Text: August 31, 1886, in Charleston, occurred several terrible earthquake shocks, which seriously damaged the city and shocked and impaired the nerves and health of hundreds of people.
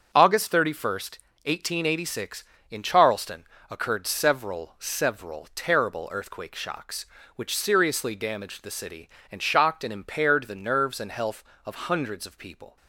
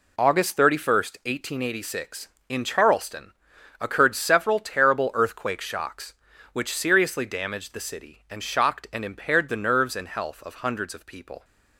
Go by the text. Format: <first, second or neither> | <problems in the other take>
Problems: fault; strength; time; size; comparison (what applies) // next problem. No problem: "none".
second | starts louder than the rest; until 1.1 s; 6.5 dB // says "several" twice; at 4.7 s